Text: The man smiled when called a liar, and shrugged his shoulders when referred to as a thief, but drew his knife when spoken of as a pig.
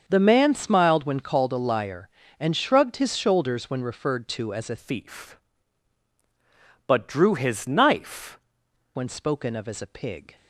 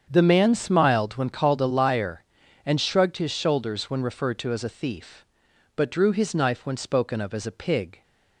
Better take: second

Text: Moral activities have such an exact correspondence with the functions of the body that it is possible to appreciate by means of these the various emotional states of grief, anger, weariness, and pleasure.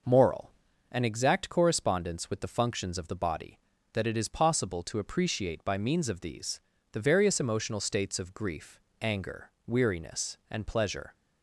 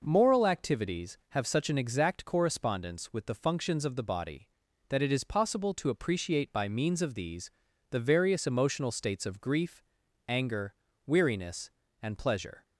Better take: second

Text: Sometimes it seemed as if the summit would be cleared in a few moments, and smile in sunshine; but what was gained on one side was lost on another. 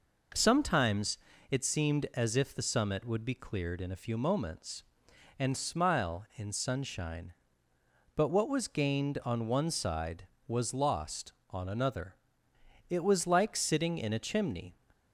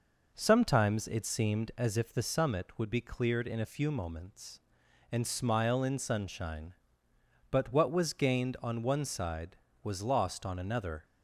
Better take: second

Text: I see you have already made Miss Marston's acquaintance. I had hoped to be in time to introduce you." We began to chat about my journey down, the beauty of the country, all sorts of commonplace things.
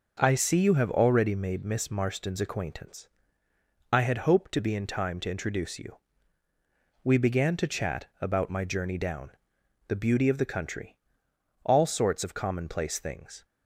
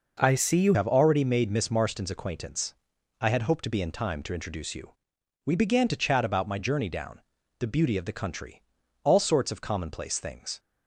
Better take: first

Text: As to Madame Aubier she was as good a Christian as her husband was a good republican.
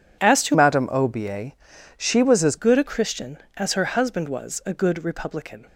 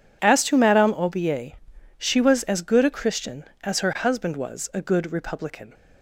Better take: second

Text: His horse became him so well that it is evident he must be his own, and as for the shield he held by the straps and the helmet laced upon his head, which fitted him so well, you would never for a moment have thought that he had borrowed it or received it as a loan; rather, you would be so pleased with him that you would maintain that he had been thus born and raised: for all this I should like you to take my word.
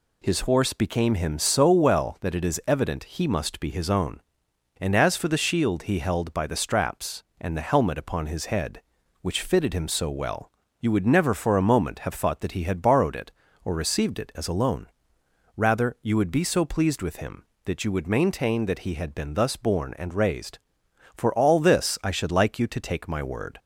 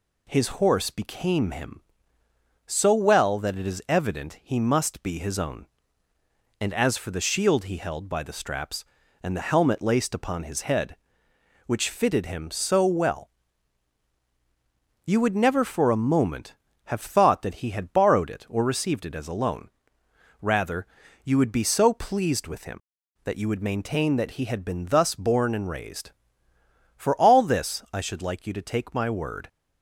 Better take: second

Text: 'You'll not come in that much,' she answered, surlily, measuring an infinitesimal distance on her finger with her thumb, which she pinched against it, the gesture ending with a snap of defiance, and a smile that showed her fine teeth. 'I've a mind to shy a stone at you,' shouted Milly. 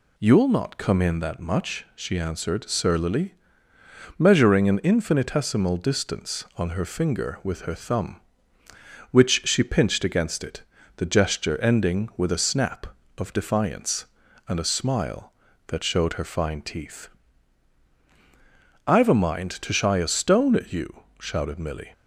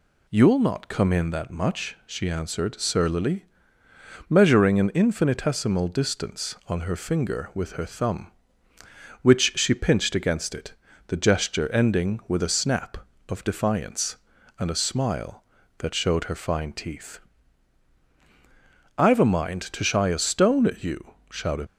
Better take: first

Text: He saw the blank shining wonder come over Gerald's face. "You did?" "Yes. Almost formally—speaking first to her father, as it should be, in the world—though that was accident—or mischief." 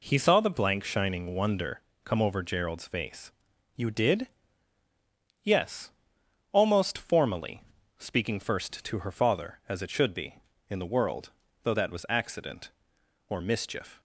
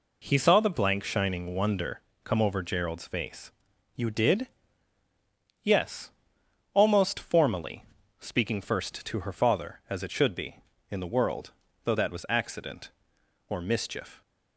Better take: neither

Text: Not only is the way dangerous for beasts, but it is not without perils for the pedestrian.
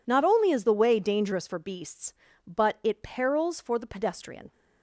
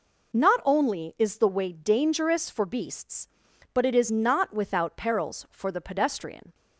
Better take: second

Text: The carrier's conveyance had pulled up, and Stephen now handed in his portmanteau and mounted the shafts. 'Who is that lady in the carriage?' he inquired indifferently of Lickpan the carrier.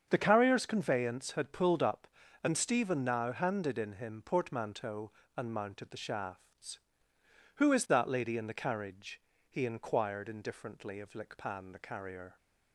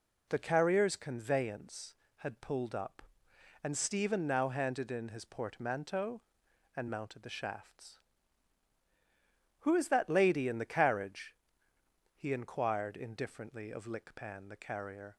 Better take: second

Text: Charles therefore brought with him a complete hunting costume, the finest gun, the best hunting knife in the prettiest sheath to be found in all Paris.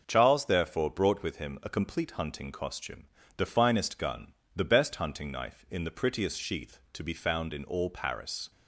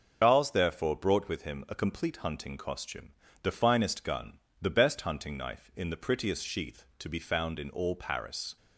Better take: first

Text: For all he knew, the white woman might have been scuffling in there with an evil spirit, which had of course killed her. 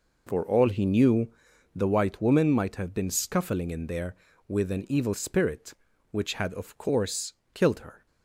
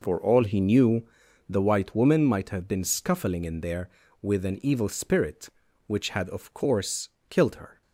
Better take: neither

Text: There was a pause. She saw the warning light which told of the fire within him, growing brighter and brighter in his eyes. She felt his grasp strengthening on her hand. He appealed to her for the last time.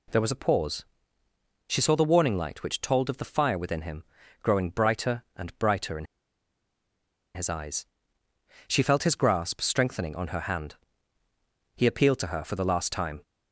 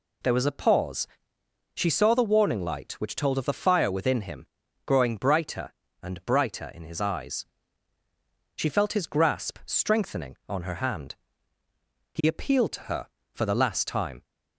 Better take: second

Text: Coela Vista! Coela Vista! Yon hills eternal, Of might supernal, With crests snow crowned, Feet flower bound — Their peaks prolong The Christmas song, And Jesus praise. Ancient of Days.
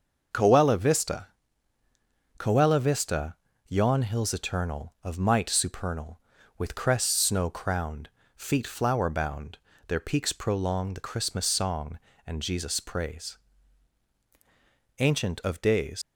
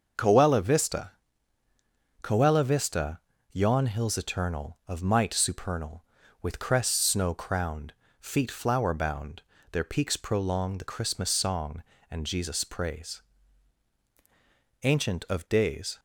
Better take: second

